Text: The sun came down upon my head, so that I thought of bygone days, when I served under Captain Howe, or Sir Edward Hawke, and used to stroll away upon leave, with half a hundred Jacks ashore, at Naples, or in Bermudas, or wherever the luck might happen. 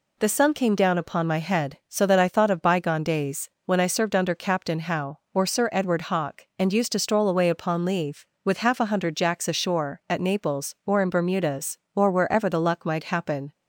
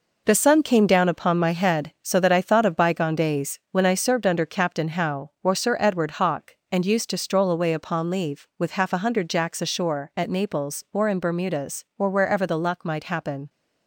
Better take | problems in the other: first | gets quieter; strong; throughout; 7.5 dB

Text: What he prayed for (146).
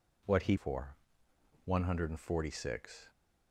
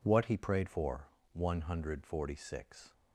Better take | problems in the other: second | skips "prayed"; at 0.5 s

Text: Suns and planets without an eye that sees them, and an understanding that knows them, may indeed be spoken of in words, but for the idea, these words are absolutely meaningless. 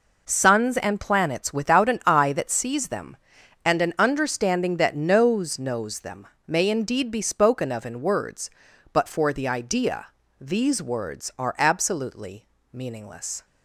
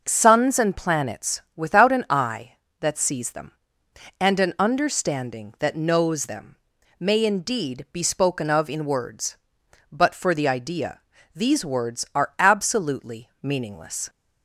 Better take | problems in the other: second | says "knows" twice; at 5.5 s // pauses between "absolutely" and "meaningless"; slight; at 12.4 s; 0.26 s long

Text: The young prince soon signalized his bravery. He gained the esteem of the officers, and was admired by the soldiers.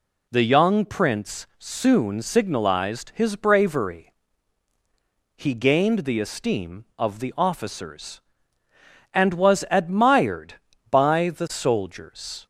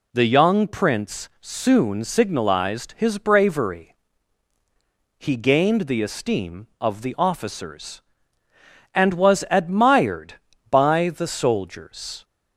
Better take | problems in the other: neither | none

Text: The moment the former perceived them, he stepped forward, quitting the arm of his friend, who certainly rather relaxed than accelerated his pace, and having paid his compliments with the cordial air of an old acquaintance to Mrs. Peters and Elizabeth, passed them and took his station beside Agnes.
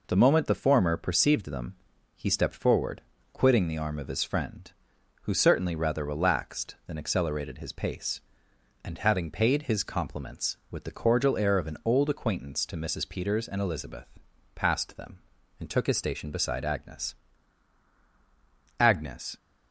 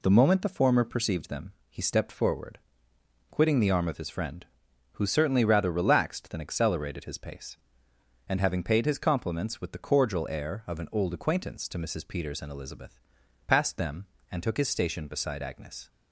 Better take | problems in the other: second | says "Agnes" twice; at 18.7 s

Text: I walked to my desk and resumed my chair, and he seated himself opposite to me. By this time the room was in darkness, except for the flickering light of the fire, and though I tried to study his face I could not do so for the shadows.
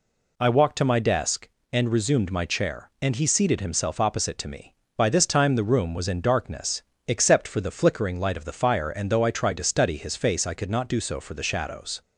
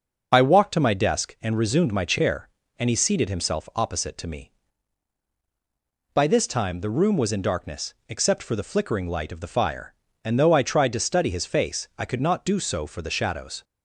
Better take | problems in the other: first | loses the start of "I"; at 0.3 s; 35 ms // starts louder than the rest; until 1.3 s; 6 dB

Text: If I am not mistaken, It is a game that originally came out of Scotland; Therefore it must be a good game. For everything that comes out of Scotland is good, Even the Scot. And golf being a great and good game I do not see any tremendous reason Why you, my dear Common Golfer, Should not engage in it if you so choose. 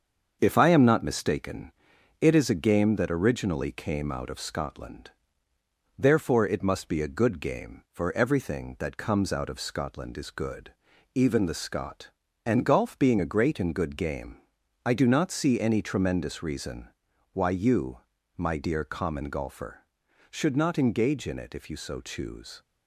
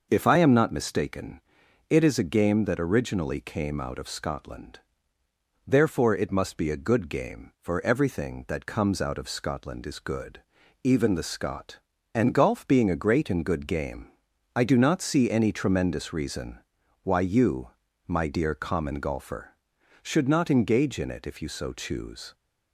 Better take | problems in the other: second | gets quieter; throughout; 3.5 dB // pauses between "game" and "I"; noticeable; at 14.3 s; 0.48 s long; noticeable in the second // pauses between "reason" and "Why"; at 16.8 s; 0.44 s long; also in the second

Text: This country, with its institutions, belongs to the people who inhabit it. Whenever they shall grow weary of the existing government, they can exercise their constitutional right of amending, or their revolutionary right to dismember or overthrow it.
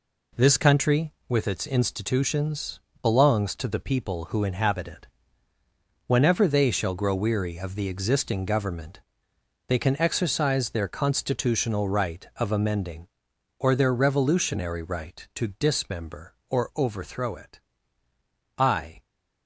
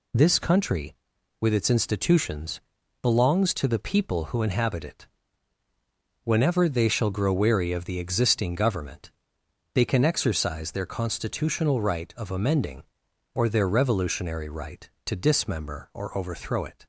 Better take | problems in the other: second | goes on to say "I"; slight; from 18.5 s on; 0.46 s long

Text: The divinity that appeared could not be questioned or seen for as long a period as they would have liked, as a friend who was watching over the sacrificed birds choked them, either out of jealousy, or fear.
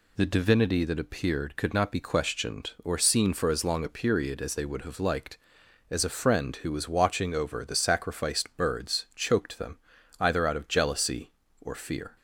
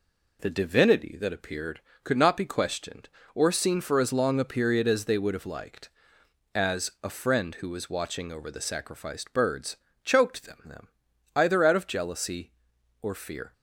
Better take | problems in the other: first | pauses between "birds" and "choked"; slight; at 9.7 s; 0.26 s long // says "them" twice; at 10.6 s

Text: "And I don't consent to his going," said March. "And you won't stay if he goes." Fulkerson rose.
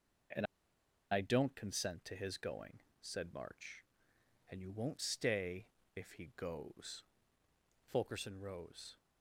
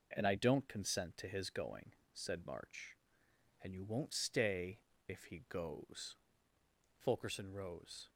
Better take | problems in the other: second | pauses between "And" and "I"; noticeable; at 0.4 s; 0.67 s long // pauses between "stay" and "if"; slight; at 5.6 s; 0.28 s long; slight in the second

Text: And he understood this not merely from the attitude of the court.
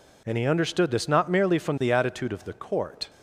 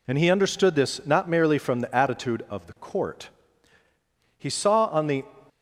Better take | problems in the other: first | goes on to say "He saw on the"; noticeable; from 4.3 s on; 0.86 s long

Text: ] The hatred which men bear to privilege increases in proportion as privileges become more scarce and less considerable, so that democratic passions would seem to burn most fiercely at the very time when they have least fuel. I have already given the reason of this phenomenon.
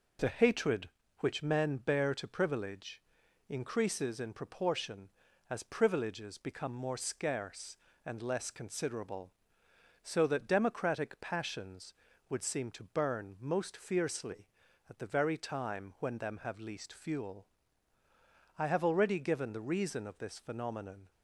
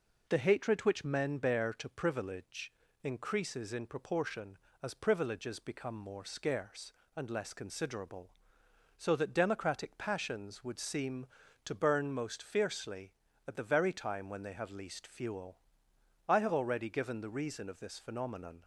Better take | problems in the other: second | pauses between "privilege" and "increases"; noticeable; at 3.0 s; 0.48 s long; slight in the second // says "them" for "they"; at 16.1 s

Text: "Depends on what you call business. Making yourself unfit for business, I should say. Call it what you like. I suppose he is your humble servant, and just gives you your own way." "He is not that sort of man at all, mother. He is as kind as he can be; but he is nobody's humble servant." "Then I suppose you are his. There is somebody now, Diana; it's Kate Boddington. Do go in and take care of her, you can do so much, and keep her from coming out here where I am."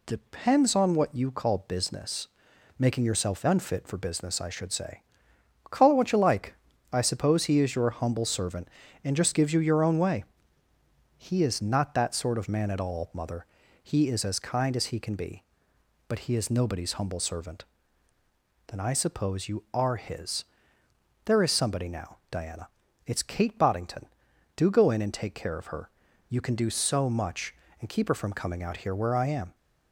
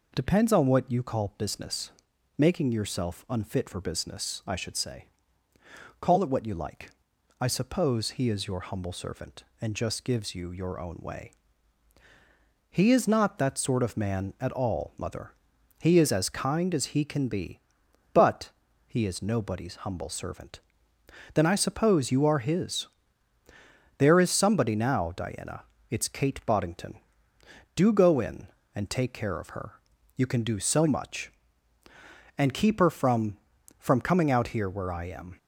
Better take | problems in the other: first | pauses between "but" and "he"; slight; at 18.5 s; 0.36 s long // says "from" twice; at 33.7 s

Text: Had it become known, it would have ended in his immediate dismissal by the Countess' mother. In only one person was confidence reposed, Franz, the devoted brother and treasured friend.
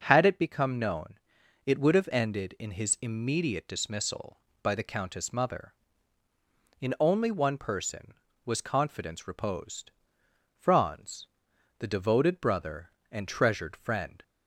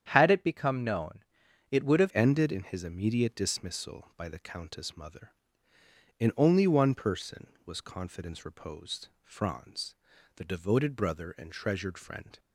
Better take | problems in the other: first | starts louder than the rest; strong; until 1.1 s; 9 dB // changes voice at "ended"; from 2.1 s on; 10.2 s long

